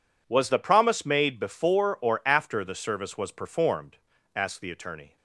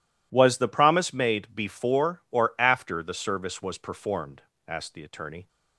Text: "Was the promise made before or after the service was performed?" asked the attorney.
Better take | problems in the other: neither | none

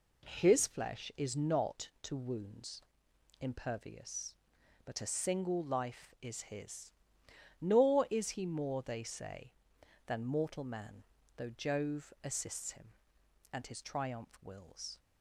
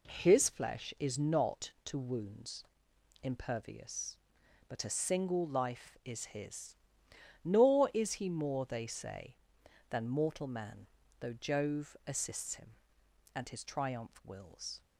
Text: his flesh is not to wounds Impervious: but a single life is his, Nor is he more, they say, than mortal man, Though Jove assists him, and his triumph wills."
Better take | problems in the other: neither | pauses between "wounds" and "Impervious"; noticeable; the same in both

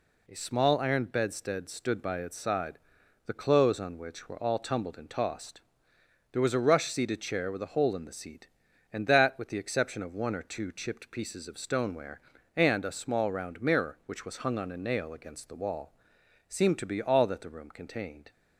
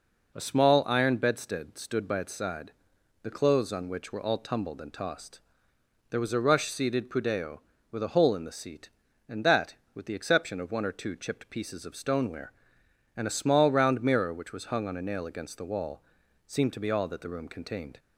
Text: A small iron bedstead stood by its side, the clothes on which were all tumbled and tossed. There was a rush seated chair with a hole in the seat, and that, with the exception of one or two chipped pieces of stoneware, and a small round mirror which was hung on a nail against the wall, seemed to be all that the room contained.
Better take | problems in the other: first | says "pudeo" for "chair"; at 7.0 s

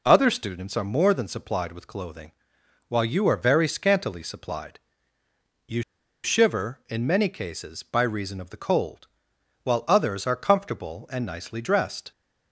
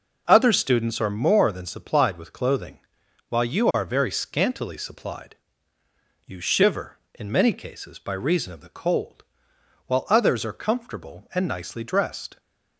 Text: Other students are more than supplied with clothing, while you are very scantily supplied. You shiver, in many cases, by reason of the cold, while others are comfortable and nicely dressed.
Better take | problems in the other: second | pauses between "You" and "shiver"; at 5.8 s; 0.41 s long

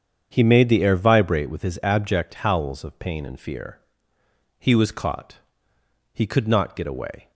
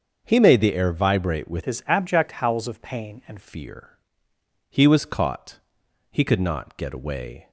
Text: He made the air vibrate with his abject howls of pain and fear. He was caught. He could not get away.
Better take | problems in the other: first | starts louder than the rest; until 1.2 s; 6.5 dB; strong in the first // changes voice from "his" to "and"; from 1.6 to 3.3 s; 1.7 s long

